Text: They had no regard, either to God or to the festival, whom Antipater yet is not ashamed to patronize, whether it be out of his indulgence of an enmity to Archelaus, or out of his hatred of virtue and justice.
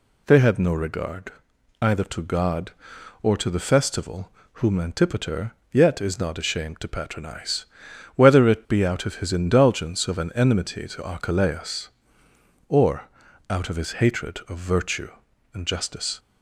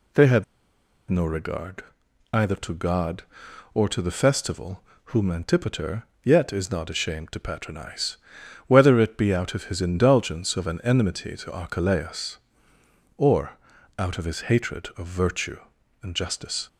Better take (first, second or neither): first